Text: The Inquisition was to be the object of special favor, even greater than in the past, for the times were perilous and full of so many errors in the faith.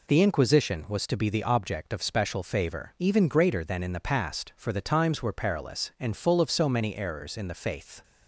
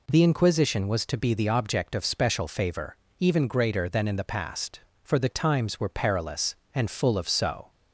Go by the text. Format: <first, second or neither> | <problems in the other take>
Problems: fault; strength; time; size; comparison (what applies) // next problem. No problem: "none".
first | stops before "many errors in the faith"; at 7.6 s